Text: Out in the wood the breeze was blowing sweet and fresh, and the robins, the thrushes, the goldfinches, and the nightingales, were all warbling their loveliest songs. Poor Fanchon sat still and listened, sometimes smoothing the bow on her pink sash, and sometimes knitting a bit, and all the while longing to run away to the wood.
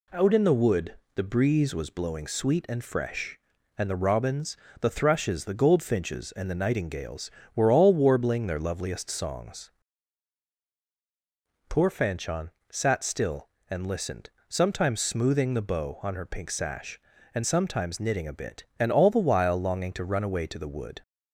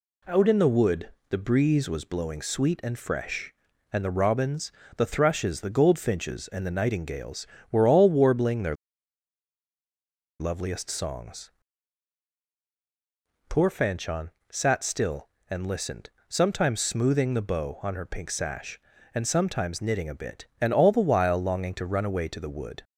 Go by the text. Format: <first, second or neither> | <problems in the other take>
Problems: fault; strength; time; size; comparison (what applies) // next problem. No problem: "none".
first | pauses between "wood" and "the"; slight; at 1.0 s; 0.22 s long; slight in the first // pauses between "their" and "loveliest"; strong; at 8.7 s; 1.6 s long // pauses between "Fanchon" and "sat"; slight; at 14.3 s; 0.20 s long; slight in the first